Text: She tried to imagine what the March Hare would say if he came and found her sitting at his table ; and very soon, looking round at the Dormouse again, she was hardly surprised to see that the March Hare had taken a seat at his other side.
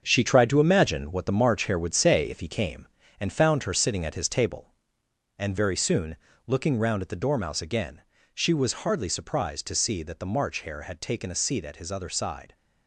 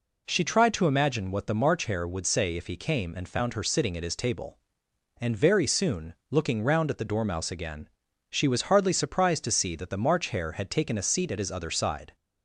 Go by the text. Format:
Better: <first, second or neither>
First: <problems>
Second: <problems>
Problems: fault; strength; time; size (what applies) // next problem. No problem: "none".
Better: second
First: gets quieter; strong; throughout; 8 dB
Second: none